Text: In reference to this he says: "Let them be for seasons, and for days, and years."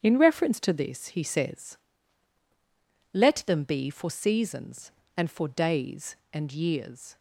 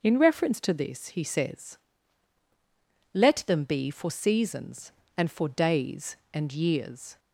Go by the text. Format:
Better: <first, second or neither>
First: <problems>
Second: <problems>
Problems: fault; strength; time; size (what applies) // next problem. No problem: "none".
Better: second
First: gets quieter; strong; throughout; 9.5 dB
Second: none